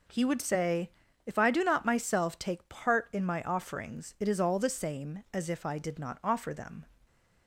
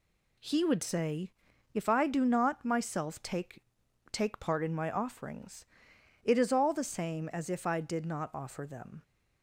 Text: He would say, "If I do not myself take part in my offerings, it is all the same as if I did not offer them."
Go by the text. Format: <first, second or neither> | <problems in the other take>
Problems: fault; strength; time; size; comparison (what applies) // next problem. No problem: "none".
first | says "take" twice; at 4.1 s